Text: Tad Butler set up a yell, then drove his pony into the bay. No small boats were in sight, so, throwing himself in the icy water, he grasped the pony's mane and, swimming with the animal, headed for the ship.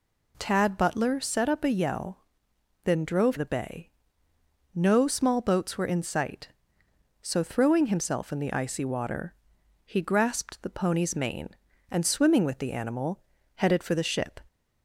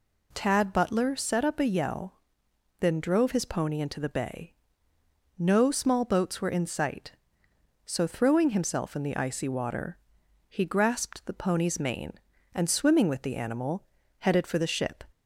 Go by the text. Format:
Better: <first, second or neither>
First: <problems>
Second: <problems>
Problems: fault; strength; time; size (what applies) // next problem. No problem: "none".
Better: second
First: skips "his pony into"; at 3.3 s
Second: none